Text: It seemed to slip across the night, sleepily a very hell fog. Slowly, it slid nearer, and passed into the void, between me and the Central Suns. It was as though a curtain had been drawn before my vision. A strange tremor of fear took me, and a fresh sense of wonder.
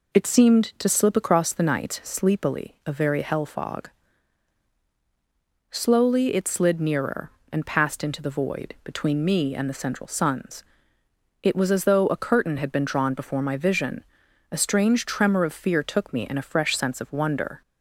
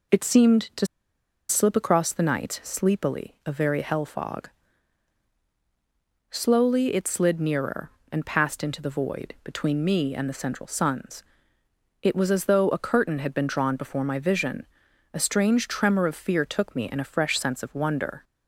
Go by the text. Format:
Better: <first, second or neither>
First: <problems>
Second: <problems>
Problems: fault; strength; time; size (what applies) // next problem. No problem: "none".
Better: first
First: none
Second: pauses between "to" and "slip"; noticeable; at 0.8 s; 0.62 s long